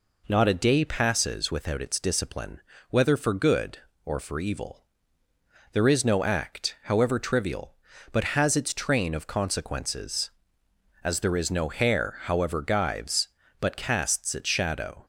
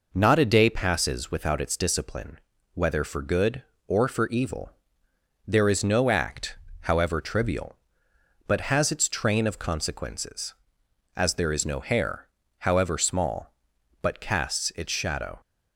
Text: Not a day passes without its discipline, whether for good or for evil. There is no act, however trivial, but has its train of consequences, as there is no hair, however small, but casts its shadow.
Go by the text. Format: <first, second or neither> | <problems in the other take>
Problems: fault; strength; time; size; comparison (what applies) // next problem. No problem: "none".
second | says "gyves" for "small"; at 12.6 s